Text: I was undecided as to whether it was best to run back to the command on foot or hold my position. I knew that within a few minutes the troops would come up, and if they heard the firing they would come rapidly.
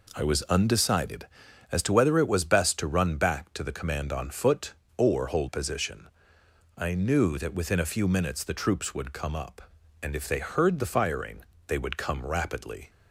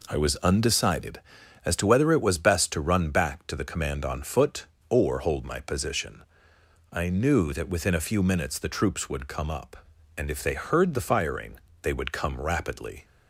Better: second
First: skips "my"; at 5.4 s // pauses between "firing" and "they"; slight; at 11.4 s; 0.24 s long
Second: pauses between "firing" and "they"; slight; at 11.5 s; 0.24 s long

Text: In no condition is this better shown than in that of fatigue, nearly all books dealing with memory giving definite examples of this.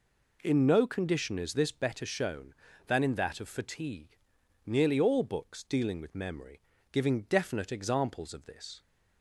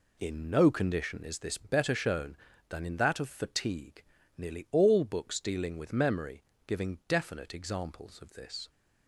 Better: neither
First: pauses between "memory" and "giving"; slight; at 6.6 s; 0.30 s long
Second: pauses between "memory" and "giving"; slight; at 6.4 s; 0.24 s long

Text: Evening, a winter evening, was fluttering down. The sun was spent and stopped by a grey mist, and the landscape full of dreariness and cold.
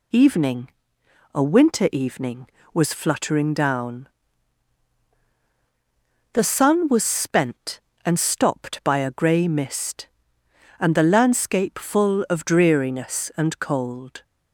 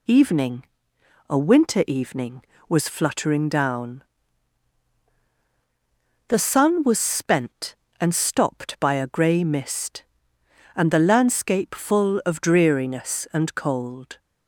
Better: neither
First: none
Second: none

